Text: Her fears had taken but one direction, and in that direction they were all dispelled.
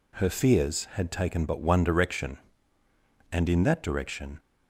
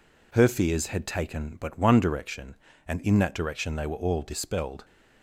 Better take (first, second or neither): second